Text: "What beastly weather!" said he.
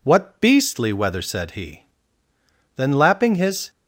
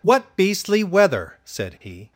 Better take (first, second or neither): second